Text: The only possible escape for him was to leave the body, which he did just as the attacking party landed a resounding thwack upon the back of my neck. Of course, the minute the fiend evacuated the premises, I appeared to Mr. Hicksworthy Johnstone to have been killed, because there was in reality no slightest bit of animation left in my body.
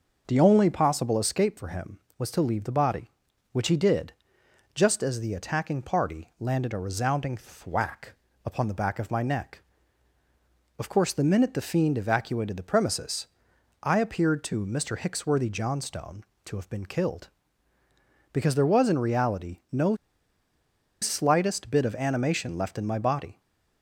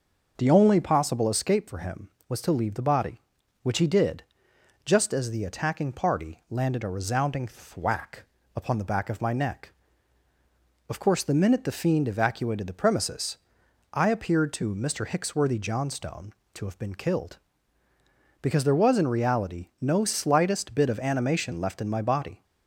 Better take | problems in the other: second | pauses between "did" and "just"; noticeable; at 4.1 s; 0.60 s long; noticeable in the second // pauses between "thwack" and "upon"; slight; at 8.1 s; 0.34 s long; slight in the second // pauses between "no" and "slightest"; at 19.9 s; 1.0 s long

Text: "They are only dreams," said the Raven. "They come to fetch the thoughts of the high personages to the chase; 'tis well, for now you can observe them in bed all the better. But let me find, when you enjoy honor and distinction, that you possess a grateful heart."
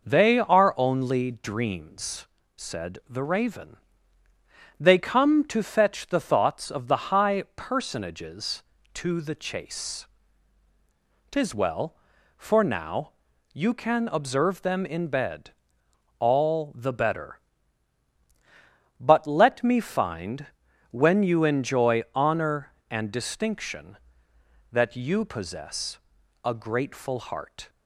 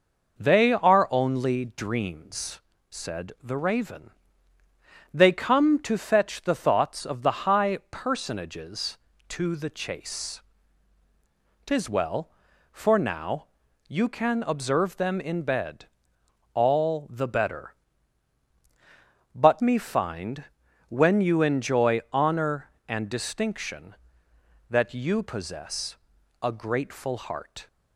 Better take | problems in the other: first | pauses between "now" and "you"; at 13.4 s; 0.42 s long; also in the first // pauses between "bed" and "all"; noticeable; at 15.8 s; 0.66 s long; noticeable in the first // skips "let"; at 19.6 s // pauses between "possess" and "a"; at 25.9 s; 0.44 s long; also in the first

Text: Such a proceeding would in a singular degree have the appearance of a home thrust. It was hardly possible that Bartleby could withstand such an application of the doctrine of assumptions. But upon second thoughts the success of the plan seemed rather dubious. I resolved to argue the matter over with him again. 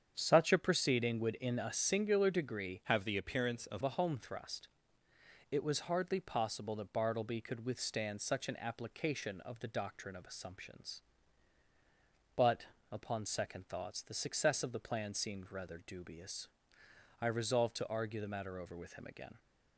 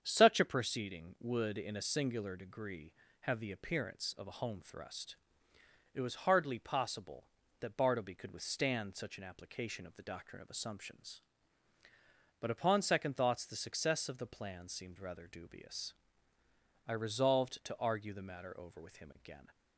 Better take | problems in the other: second | starts louder than the rest; strong; until 1.1 s; 8 dB; strong in the second // changes voice from "have" to "of"; from 2.8 to 3.8 s; 1.0 s long // pauses between "But" and "upon"; slight; at 12.6 s; 0.26 s long

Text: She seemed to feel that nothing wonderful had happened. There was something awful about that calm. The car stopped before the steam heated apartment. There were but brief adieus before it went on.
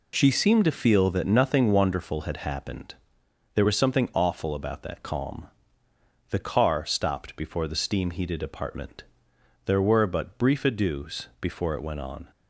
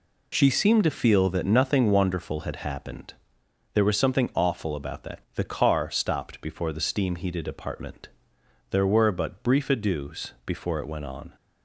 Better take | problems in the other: first | skips "calm"; at 5.2 s

